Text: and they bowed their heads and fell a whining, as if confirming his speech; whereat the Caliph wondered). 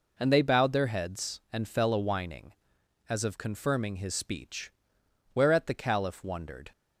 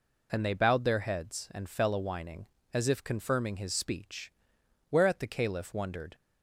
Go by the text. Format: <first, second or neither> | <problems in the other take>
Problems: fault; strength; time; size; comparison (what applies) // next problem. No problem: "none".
second | says "of" for "if"; at 3.2 s